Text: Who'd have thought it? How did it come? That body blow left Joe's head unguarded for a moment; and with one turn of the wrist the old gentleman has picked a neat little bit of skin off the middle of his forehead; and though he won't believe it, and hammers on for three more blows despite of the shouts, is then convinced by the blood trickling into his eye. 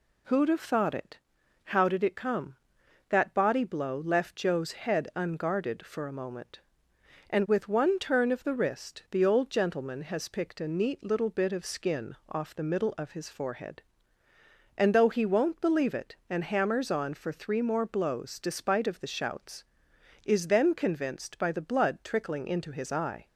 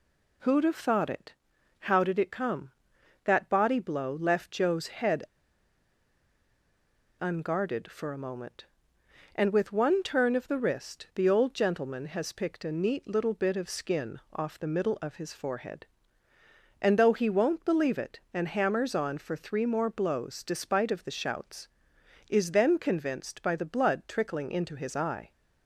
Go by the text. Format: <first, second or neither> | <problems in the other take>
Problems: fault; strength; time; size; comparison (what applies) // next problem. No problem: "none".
first | pauses between "head" and "unguarded"; strong; at 5.2 s; 1.9 s long